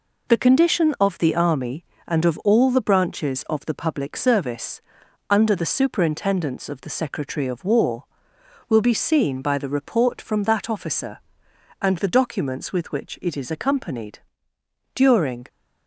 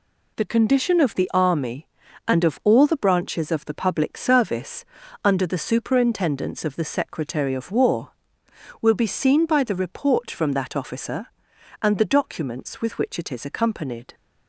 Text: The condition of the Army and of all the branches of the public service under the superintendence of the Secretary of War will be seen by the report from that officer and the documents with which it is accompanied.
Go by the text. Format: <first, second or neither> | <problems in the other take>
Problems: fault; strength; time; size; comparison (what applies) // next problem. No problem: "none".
second | pauses between "service" and "under"; noticeable; at 4.8 s; 0.48 s long; also in the second // goes on to say "During"; from 14.9 s on; 0.54 s long